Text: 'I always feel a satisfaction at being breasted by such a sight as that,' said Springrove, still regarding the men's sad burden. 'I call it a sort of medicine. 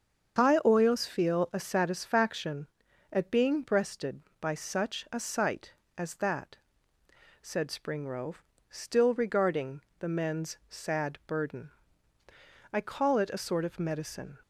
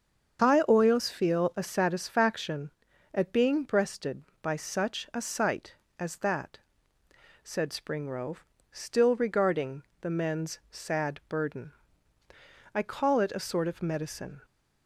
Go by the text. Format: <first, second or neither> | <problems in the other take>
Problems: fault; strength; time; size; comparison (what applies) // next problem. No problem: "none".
neither | starts louder than the rest; the same in both // pauses between "regarding" and "the"; slight; the same in both